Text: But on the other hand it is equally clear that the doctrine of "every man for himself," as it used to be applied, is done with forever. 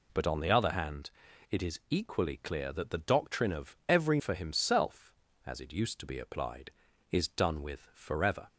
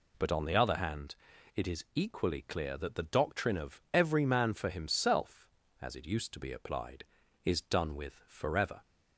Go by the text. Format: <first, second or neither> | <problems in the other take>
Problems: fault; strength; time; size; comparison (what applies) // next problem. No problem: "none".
second | pauses between "hand" and "it"; at 1.1 s; 0.40 s long; also in the second // skips "man"; at 4.1 s